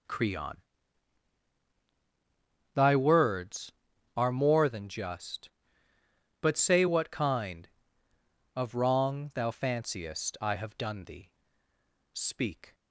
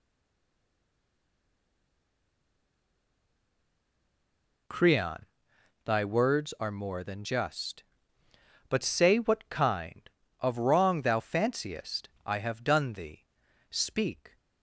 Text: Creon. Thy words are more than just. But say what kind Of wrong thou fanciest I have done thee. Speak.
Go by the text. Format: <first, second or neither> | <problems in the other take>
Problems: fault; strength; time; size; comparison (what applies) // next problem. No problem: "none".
first | stays silent before the first word; strong; until 4.6 s; 4.6 s long // pauses between "fanciest" and "I"; slight; at 12.0 s; 0.16 s long